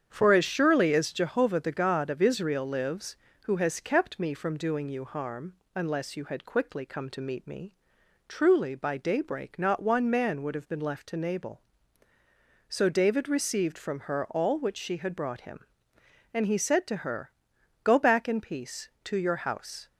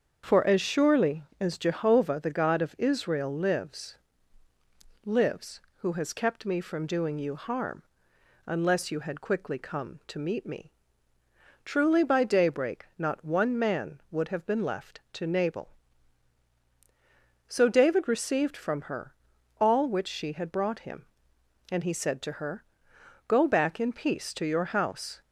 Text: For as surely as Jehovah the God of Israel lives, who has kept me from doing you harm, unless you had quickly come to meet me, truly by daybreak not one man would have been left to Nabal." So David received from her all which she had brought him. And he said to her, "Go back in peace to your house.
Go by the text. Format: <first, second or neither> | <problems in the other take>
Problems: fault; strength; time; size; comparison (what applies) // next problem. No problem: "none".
first | starts louder than the rest; until 1.4 s; 7 dB; strong in the first // says "lives" twice; at 5.0 s // pauses between "her" and "all"; noticeable; at 19.1 s; 0.48 s long